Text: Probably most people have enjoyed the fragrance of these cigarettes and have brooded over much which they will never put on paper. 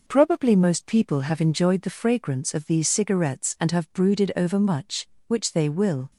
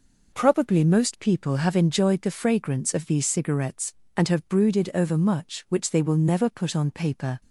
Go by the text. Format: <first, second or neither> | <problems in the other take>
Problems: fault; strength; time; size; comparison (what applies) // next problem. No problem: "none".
second | stops before "never put on paper"; at 6.1 s